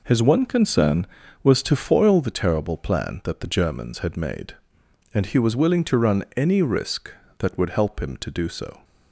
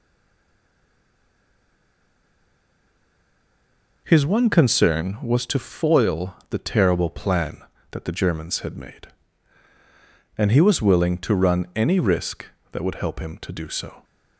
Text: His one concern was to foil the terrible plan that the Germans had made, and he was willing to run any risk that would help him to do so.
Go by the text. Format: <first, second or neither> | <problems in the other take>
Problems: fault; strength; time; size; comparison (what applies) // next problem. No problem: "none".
first | stays silent before the first word; strong; until 4.0 s; 4.0 s long